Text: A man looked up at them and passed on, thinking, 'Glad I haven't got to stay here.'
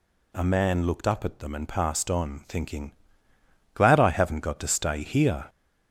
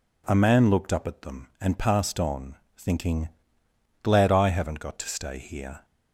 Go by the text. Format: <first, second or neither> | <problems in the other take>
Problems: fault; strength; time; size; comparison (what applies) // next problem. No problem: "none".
second | gets louder; noticeable; throughout; 4 dB